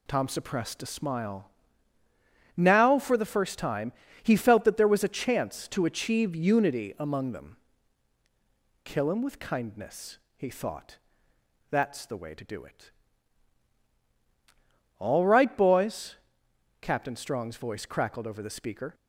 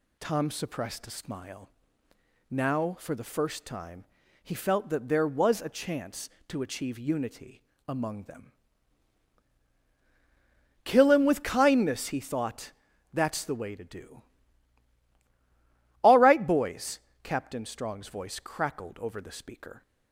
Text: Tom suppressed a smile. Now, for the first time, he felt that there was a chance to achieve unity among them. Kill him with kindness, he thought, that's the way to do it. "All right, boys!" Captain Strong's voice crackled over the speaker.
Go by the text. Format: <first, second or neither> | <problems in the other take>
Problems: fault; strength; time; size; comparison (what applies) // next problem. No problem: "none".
first | pauses between "unity" and "among"; slight; at 7.6 s; 0.26 s long // skips "it"; at 15.1 s